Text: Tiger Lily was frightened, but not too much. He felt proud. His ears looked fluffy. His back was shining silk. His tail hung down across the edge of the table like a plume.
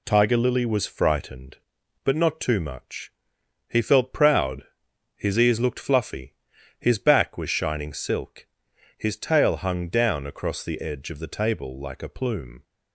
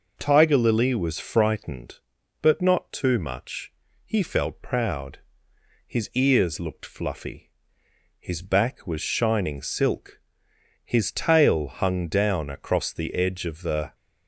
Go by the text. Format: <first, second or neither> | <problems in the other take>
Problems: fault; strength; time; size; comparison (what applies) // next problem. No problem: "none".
first | stops before "table like a plume"; at 13.9 s